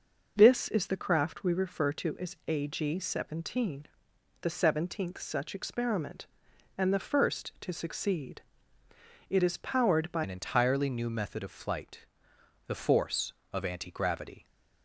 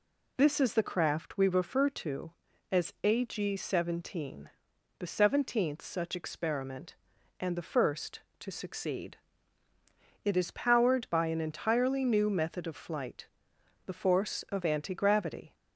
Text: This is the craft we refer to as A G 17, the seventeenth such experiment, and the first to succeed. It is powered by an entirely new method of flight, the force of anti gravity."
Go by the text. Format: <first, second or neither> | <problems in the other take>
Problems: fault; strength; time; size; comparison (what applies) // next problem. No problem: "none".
second | changes voice at "an"; from 10.2 s on; 4.2 s long